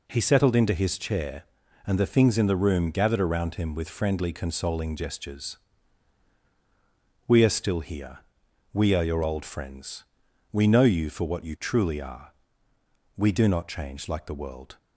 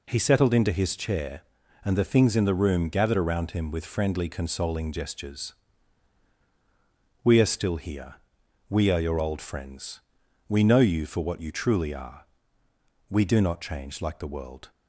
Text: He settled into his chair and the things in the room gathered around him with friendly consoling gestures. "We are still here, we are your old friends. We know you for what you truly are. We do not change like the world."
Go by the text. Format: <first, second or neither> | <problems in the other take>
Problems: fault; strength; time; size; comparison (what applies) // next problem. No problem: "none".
neither | none